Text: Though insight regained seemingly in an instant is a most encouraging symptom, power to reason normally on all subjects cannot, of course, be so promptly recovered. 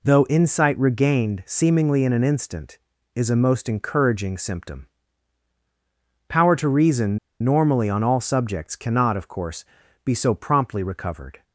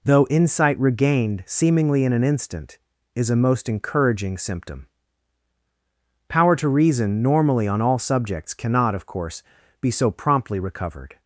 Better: second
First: pauses between "reason" and "normally"; slight; at 7.1 s; 0.24 s long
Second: none

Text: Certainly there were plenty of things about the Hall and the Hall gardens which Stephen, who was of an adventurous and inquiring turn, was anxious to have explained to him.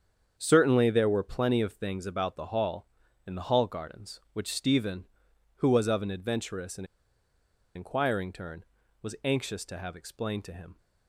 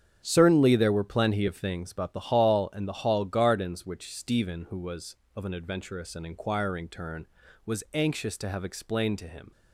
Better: second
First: starts louder than the rest; strong; until 1.3 s; 7.5 dB // pauses between "and" and "inquiring"; noticeable; at 6.8 s; 0.89 s long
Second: starts louder than the rest; strong; until 1.2 s; 8.5 dB

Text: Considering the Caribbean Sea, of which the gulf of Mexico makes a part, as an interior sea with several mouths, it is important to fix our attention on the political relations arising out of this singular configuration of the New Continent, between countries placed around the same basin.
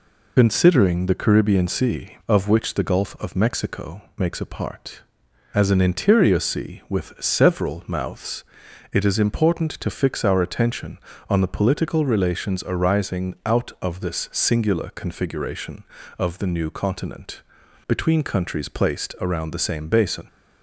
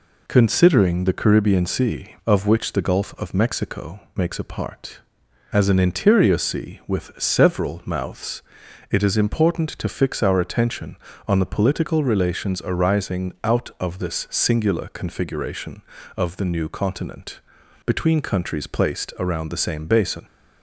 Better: second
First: loses the start of "Considering"; at 0.3 s; 70 ms // pauses between "Mexico" and "makes"; slight; at 4.0 s; 0.16 s long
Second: pauses between "Mexico" and "makes"; slight; at 4.0 s; 0.16 s long

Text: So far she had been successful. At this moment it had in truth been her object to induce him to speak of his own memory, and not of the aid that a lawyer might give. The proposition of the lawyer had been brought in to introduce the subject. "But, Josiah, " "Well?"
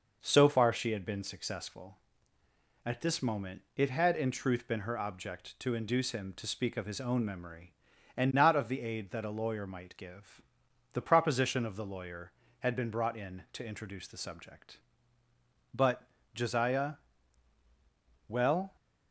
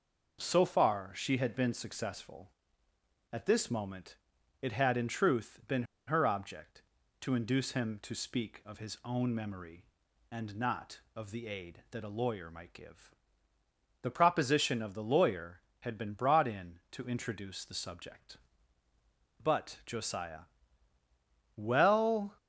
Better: first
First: none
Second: pauses between "moment" and "it"; noticeable; at 4.1 s; 0.46 s long // pauses between "been" and "her"; slight; at 5.8 s; 0.23 s long

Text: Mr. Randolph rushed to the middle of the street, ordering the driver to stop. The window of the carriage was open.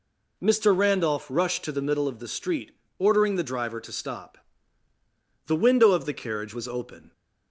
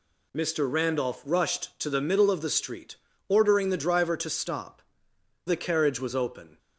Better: first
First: none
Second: skips "The window of"; at 5.1 s

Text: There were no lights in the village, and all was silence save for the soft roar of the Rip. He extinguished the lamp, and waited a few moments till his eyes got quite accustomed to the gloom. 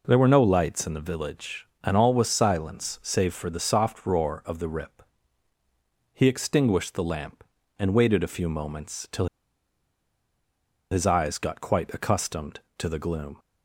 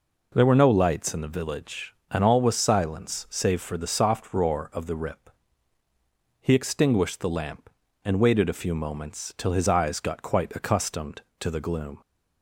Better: second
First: pauses between "till" and "his"; strong; at 9.2 s; 1.6 s long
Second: none

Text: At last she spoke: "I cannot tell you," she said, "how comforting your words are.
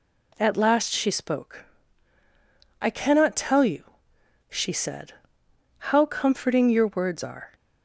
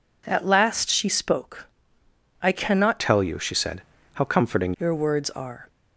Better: first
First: none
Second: changes voice from "tell" to "comforting"; from 2.9 to 4.7 s; 1.8 s long

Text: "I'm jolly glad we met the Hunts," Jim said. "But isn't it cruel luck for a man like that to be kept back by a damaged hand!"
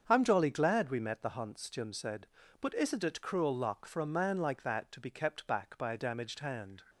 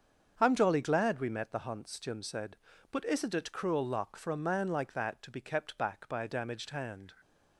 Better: neither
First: starts louder than the rest; until 1.0 s; 7 dB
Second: starts louder than the rest; until 1.3 s; 7 dB

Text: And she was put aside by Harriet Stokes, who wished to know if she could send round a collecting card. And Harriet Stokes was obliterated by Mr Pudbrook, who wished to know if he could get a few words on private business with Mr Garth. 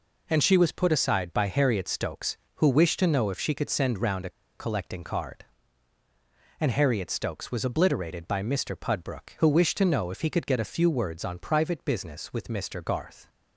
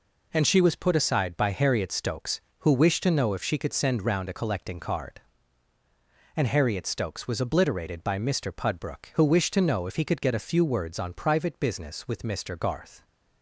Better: second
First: pauses between "a" and "collecting"; slight; at 4.3 s; 0.27 s long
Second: none

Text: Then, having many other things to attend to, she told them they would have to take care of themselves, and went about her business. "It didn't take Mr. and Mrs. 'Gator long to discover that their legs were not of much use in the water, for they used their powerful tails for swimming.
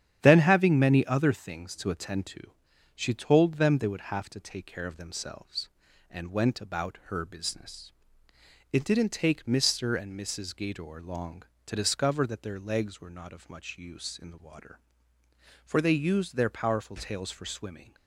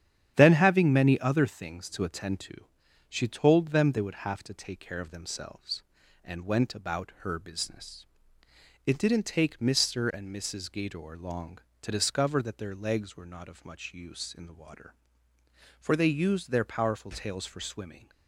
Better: neither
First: starts louder than the rest; strong; until 1.2 s; 10 dB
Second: starts louder than the rest; strong; until 1.3 s; 10 dB

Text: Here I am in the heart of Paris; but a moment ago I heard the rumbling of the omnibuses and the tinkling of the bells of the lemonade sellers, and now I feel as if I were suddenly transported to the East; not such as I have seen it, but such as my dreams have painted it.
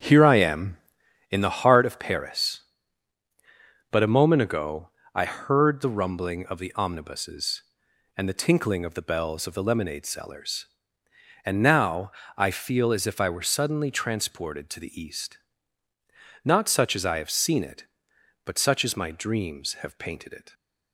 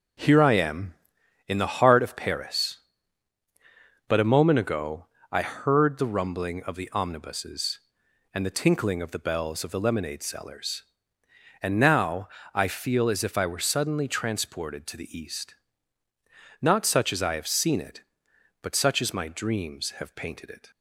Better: second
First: starts louder than the rest; strong; until 1.6 s; 7.5 dB // pauses between "ago" and "I"; slight; at 4.8 s; 0.24 s long // pauses between "now" and "I"; slight; at 12.1 s; 0.24 s long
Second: pauses between "ago" and "I"; slight; at 5.0 s; 0.24 s long // pauses between "now" and "I"; slight; at 12.2 s; 0.24 s long

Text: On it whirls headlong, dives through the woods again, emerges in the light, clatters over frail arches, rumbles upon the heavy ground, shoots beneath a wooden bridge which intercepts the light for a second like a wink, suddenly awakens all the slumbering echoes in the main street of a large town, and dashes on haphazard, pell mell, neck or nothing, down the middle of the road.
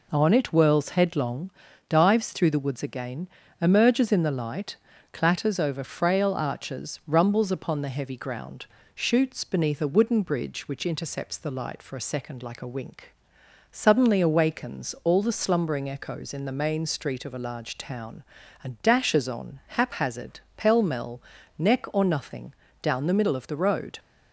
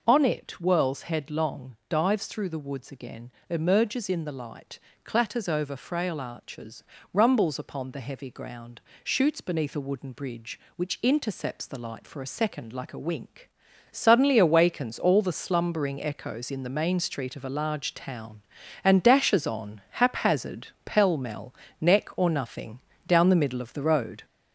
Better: first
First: none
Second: gets louder; noticeable; throughout; 4.5 dB

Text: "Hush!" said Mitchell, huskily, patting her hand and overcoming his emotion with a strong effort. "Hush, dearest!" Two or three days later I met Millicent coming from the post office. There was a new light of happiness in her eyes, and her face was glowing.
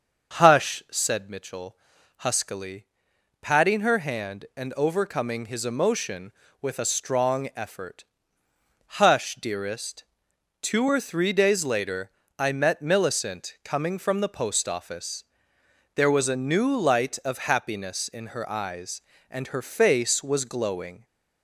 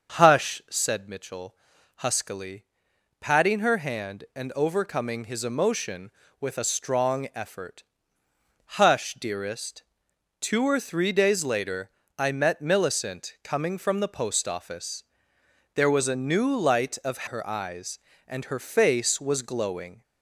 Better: first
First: starts louder than the rest; until 1.4 s; 6.5 dB // pauses between "later" and "I"; slight; at 12.1 s; 0.28 s long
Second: starts louder than the rest; until 1.2 s; 6.5 dB // pauses between "later" and "I"; slight; at 11.9 s; 0.28 s long // skips "happiness in"; at 17.2 s

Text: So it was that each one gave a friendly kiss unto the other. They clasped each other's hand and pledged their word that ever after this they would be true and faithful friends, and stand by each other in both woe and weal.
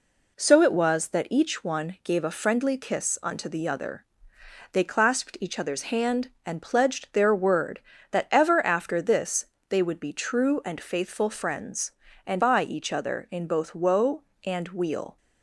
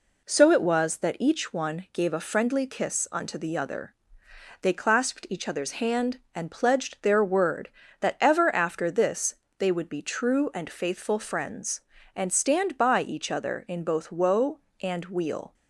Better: second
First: pauses between "this" and "they"; slight; at 9.4 s; 0.22 s long // skips "stand"; at 12.4 s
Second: pauses between "this" and "they"; slight; at 9.3 s; 0.22 s long

